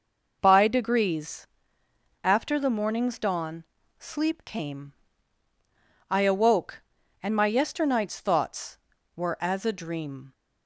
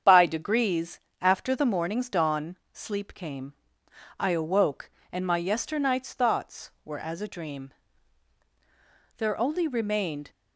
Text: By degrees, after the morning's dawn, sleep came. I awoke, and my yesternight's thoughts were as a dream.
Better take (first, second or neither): first